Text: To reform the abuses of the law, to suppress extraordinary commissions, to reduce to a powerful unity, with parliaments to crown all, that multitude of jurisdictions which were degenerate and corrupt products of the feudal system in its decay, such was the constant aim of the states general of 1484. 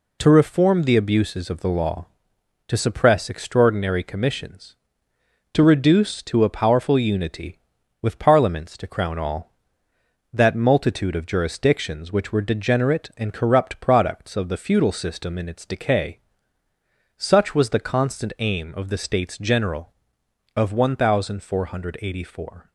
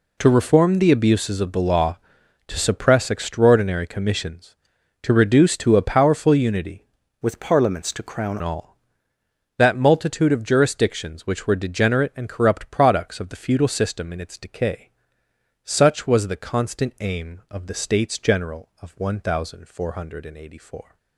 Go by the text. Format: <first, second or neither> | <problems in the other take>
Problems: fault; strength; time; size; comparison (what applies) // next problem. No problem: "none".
first | changes voice from "with" to "crown"; from 7.2 to 8.3 s; 1.1 s long